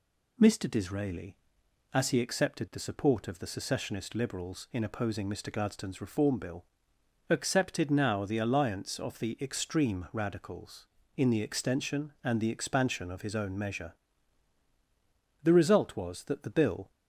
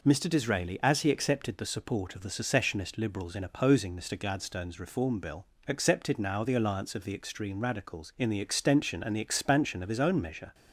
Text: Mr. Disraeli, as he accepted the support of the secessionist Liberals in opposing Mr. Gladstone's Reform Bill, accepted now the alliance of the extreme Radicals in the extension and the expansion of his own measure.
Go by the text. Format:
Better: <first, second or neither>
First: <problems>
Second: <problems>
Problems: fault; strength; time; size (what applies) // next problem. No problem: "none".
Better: second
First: goes on to say "The result was that the bill"; from 15.4 s on; 1.4 s long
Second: none